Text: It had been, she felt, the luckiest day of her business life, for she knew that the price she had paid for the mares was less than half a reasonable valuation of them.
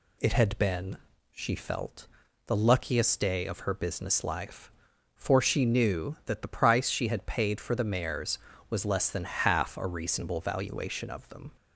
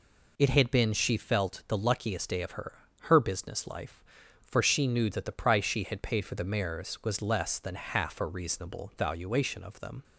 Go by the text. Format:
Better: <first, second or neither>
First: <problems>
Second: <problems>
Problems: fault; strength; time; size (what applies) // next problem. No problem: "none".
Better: first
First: none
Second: says "her" twice; at 3.0 s